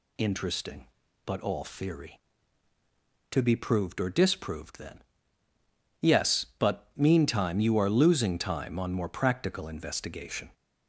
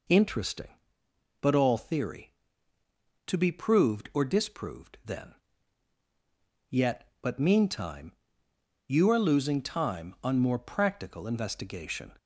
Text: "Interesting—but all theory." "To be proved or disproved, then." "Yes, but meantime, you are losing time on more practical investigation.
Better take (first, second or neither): first